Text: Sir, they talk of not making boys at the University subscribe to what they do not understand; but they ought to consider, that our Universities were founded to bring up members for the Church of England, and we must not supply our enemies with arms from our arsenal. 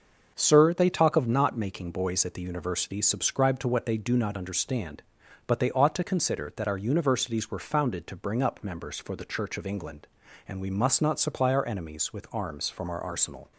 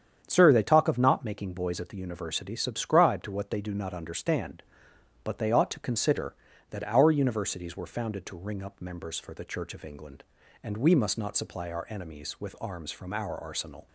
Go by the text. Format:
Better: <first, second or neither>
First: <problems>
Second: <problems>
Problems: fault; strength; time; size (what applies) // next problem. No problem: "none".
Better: first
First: starts louder than the rest; until 1.3 s; 6 dB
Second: starts louder than the rest; strong; until 1.2 s; 8.5 dB // says "ring" for "bring"; at 8.3 s